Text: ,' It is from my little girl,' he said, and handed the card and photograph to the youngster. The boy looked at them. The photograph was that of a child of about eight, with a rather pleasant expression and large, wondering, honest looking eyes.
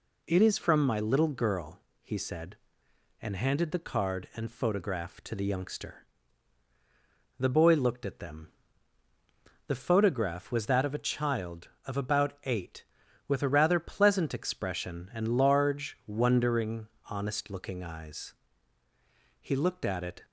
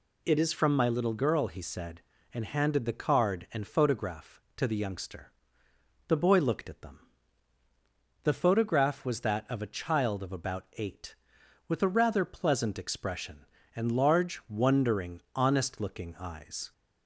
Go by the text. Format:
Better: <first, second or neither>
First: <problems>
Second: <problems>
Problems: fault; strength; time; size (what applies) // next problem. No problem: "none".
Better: second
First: goes on to say "He looked at it"; noticeable; from 19.4 s on; 0.80 s long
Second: none